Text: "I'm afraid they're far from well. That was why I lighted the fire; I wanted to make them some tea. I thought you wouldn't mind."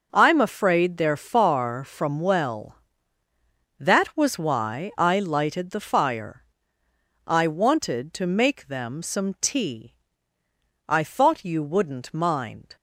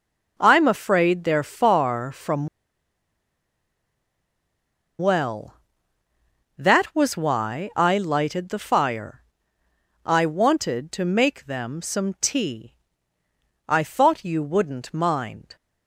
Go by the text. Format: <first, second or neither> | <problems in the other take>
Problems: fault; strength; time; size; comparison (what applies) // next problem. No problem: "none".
first | pauses between "from" and "well"; strong; at 2.4 s; 2.5 s long